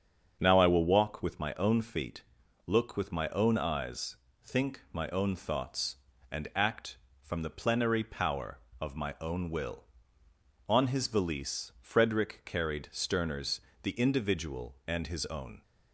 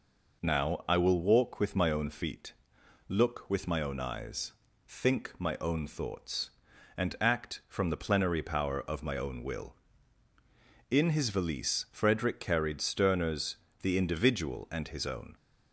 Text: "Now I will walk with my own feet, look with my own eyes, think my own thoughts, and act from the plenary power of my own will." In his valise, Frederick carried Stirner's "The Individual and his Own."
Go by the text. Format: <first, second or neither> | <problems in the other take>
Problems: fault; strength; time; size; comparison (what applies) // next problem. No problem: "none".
second | starts louder than the rest; strong; until 1.4 s; 7 dB // says "On" for "In"; at 10.6 s // pauses between "Stirner's" and "The"; slight; at 13.5 s; 0.22 s long; slight in the second